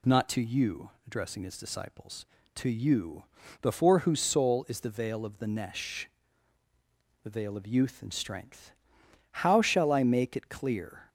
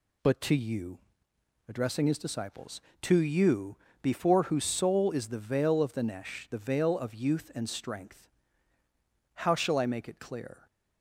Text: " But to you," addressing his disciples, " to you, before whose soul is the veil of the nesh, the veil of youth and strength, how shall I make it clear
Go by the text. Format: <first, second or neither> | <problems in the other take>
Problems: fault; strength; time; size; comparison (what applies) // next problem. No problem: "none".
second | says "Not" for "But"; at 0.0 s